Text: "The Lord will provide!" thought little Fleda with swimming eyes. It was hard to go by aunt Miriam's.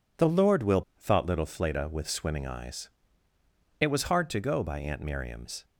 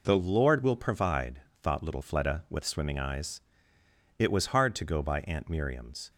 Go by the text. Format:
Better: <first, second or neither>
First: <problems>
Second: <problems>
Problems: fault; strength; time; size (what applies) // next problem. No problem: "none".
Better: second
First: skips "provide"; at 0.9 s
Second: none